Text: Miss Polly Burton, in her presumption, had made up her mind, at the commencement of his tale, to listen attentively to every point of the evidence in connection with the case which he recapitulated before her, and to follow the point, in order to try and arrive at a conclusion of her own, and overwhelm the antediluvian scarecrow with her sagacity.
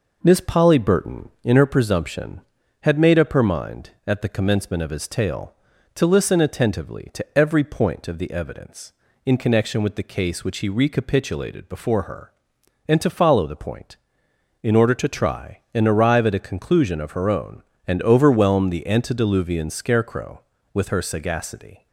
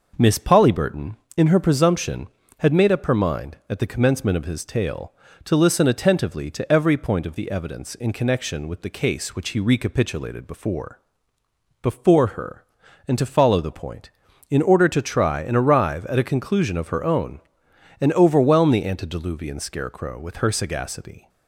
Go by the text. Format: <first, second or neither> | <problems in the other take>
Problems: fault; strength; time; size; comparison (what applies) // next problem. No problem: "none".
first | says "before" twice; at 11.8 s